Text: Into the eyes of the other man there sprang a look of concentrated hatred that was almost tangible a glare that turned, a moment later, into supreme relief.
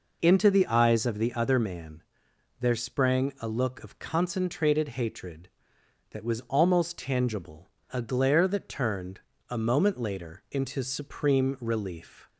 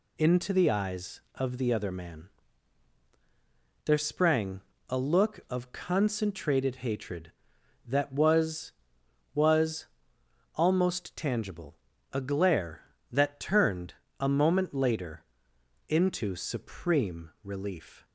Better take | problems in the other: first | pauses between "man" and "there"; strong; at 2.2 s; 1.5 s long; noticeable in the first // pauses between "sprang" and "a"; slight; at 4.6 s; 0.26 s long // says "was" twice; at 9.3 s // pauses between "tangible" and "a"; slight; at 11.7 s; 0.36 s long; slight in the first

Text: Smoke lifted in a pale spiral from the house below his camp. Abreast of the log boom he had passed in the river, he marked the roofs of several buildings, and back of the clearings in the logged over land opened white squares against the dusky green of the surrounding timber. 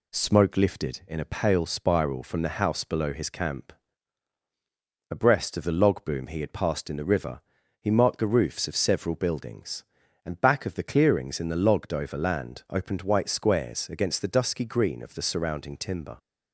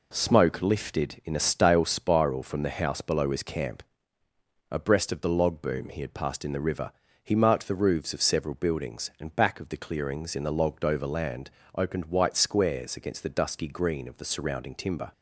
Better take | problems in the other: first | says "stale" for "pale"; at 1.3 s // pauses between "land" and "opened"; slight; at 11.4 s; 0.28 s long

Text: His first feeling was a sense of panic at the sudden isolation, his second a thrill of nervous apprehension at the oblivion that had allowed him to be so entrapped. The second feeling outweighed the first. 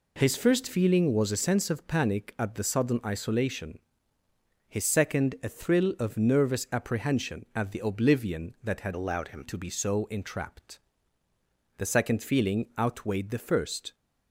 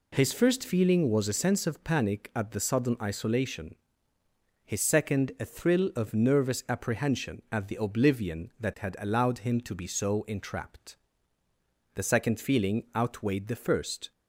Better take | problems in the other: second | changes voice from "allowed" to "him"; from 8.9 to 9.4 s; 0.5 s long

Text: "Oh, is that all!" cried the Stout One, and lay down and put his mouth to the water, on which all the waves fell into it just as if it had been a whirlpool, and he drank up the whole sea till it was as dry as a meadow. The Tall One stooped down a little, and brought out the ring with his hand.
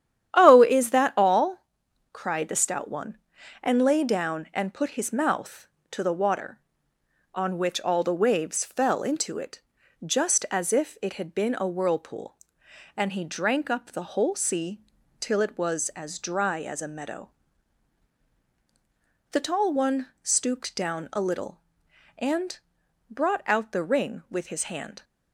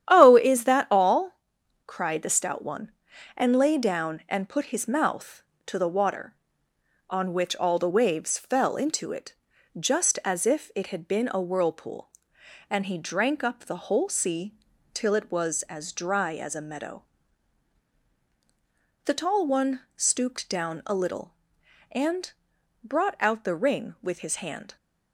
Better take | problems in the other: neither | starts louder than the rest; strong; the same in both // pauses between "it" and "just"; the same in both // pauses between "sea" and "till"; the same in both // pauses between "and" and "brought"; noticeable; the same in both

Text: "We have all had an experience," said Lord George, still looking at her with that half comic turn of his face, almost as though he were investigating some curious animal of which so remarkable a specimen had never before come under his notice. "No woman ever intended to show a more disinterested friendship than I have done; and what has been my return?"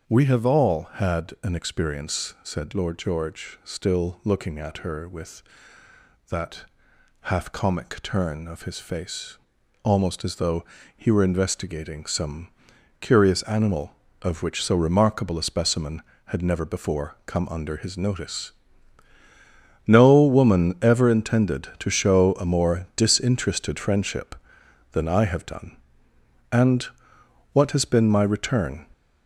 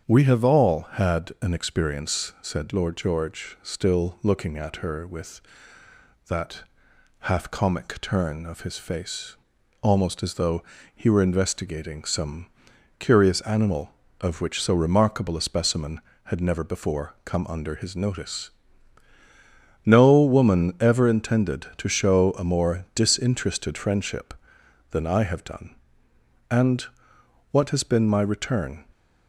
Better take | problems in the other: second | gets louder; noticeable; throughout; 5.5 dB // starts louder than the rest; until 1.1 s; 7 dB; strong in the second // pauses between "that" and "half"; noticeable; at 6.6 s; 0.56 s long; noticeable in the second // pauses between "though" and "he"; slight; at 10.6 s; 0.32 s long; slight in the second // pauses between "some" and "curious"; noticeable; at 12.4 s; 0.52 s long; noticeable in the second // pauses between "and" and "what"; noticeable; at 26.8 s; 0.66 s long; noticeable in the second

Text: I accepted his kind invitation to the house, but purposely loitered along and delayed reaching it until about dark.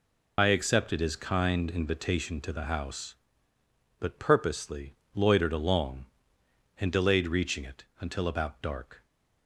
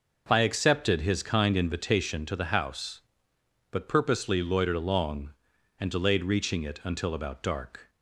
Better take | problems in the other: second | loses the start of "I"; at 0.3 s; 75 ms // pauses between "purposely" and "loitered"; slight; at 4.9 s; 0.20 s long // pauses between "it" and "until"; slight; at 7.8 s; 0.16 s long

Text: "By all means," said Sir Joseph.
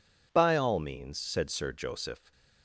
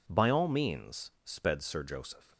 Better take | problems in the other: first | says "sped" for "said"; at 1.2 s

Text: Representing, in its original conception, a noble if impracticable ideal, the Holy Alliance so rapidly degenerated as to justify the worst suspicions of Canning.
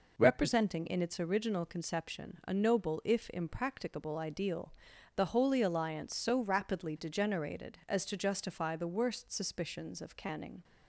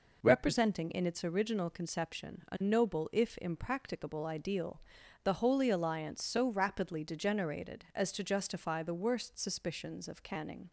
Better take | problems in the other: neither | none

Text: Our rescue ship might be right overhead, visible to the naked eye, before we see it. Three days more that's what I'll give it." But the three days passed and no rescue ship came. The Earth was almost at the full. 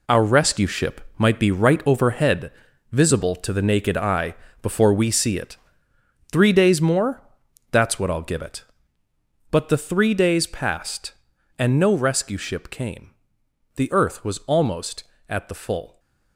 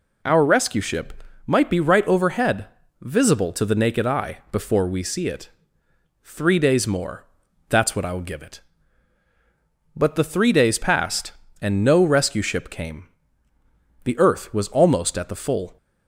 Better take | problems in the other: second | gets quieter; strong; throughout; 10.5 dB // pauses between "ship" and "might"; slight; at 1.0 s; 0.16 s long; slight in the second // pauses between "more" and "that's"; noticeable; at 7.2 s; 0.50 s long; also in the second

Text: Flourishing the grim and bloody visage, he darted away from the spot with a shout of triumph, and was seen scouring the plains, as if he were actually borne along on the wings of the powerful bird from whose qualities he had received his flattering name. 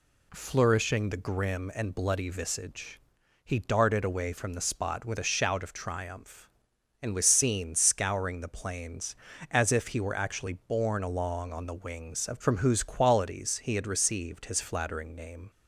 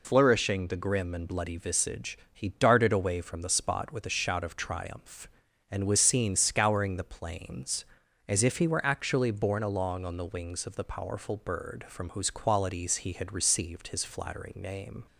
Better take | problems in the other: second | skips "the powerful bird"; at 12.3 s

